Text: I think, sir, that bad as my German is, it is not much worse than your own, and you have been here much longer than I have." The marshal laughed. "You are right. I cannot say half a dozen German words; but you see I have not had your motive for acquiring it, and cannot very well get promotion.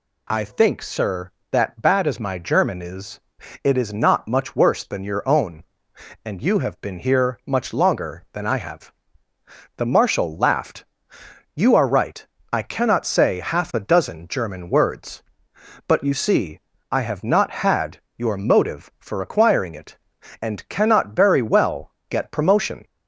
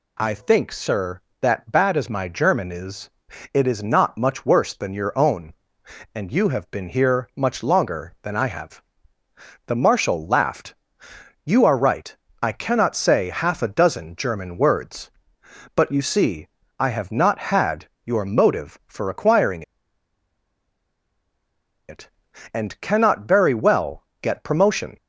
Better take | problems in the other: first | pauses between "see" and "I"; slight; at 16.4 s; 0.32 s long; slight in the first // pauses between "had" and "your"; slight; at 17.8 s; 0.18 s long; slight in the first // pauses between "acquiring" and "it"; strong; at 19.6 s; 2.2 s long // pauses between "well" and "get"; slight; at 24.0 s; 0.18 s long; slight in the first

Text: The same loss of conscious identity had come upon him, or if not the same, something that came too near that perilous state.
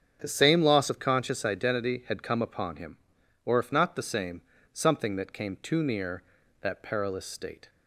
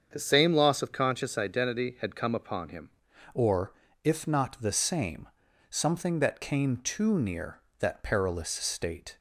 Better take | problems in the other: first | starts louder than the rest; strong; until 1.1 s; 7 dB; strong in the first // changes voice at "or"; from 3.3 s on; 5.8 s long // pauses between "or" and "if"; slight; at 3.7 s; 0.30 s long

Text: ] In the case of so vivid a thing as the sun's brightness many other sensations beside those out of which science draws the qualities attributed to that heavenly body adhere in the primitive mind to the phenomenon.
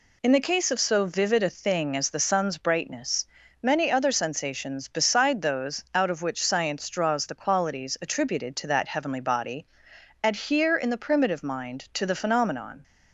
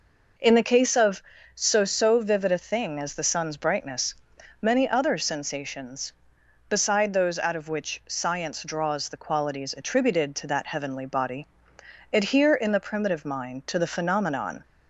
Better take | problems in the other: first | says "so" twice; at 1.8 s // pauses between "brightness" and "many"; noticeable; at 4.1 s; 0.48 s long; also in the first // pauses between "body" and "adhere"; noticeable; at 11.4 s; 0.66 s long; noticeable in the first

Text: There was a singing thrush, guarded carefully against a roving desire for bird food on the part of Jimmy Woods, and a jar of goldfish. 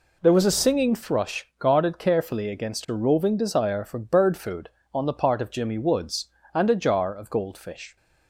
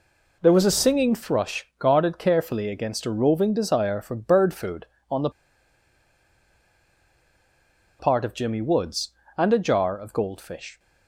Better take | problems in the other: first | pauses between "the" and "part"; strong; at 5.3 s; 2.6 s long

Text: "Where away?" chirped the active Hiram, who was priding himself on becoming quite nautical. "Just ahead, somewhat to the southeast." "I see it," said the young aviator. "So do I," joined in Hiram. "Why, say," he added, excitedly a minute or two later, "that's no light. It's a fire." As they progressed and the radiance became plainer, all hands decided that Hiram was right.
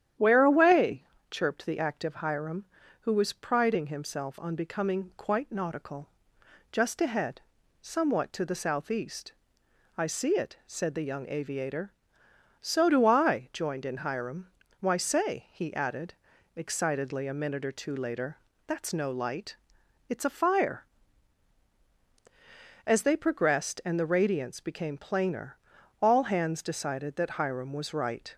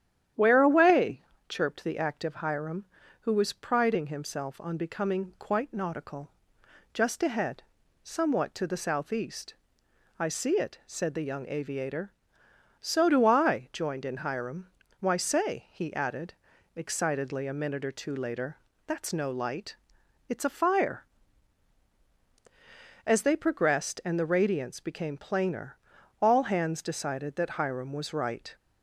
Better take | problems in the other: neither | starts louder than the rest; strong; the same in both

